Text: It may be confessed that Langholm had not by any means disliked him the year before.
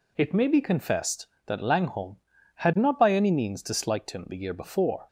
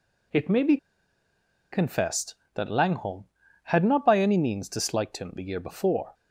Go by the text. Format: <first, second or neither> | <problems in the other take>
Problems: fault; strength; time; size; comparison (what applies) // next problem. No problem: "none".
first | pauses between "be" and "confessed"; noticeable; at 0.7 s; 0.95 s long